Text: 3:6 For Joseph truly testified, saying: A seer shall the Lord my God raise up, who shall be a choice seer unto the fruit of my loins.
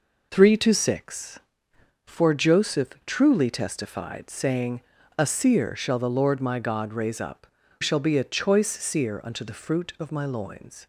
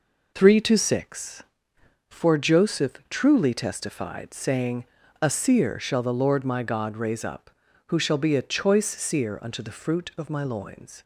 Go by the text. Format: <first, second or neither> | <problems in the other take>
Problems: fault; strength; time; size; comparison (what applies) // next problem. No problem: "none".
second | skips "who"; at 7.6 s